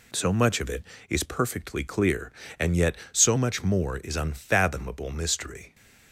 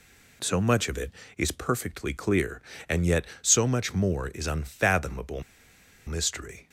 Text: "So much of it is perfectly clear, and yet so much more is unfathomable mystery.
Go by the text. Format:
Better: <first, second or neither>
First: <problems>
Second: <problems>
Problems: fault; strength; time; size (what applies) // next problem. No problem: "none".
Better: first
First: none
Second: pauses between "unfathomable" and "mystery"; noticeable; at 5.4 s; 0.65 s long